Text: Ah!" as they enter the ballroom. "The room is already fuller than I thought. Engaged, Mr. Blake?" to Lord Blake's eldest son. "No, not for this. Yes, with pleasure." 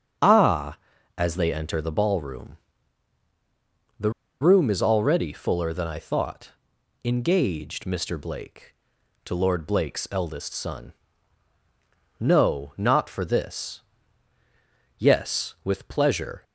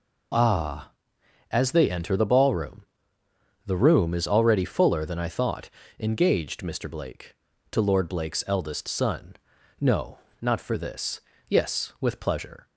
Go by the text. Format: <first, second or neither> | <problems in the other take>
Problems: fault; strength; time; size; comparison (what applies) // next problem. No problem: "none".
second | starts louder than the rest; strong; until 1.6 s; 8 dB // pauses between "The" and "room"; slight; at 4.1 s; 0.29 s long